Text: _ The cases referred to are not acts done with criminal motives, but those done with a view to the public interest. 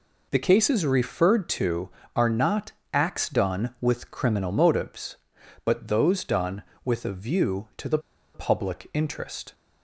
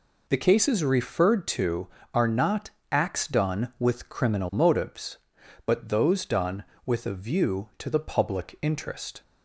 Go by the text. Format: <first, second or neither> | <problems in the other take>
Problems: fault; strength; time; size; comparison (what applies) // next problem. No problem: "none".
second | pauses between "not" and "acts"; slight; at 2.7 s; 0.20 s long; slight in the second // pauses between "the" and "public"; slight; at 7.9 s; 0.35 s long